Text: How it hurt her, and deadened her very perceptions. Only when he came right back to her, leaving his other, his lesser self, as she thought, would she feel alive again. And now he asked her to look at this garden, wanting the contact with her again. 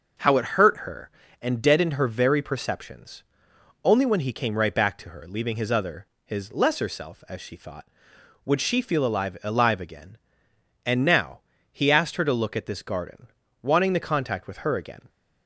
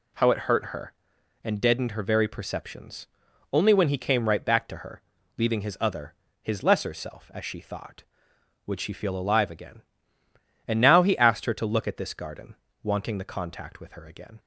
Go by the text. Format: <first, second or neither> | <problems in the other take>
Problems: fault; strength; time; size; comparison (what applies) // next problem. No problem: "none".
second | says "alive" twice; at 9.4 s // pauses between "now" and "he"; slight; at 11.3 s; 0.32 s long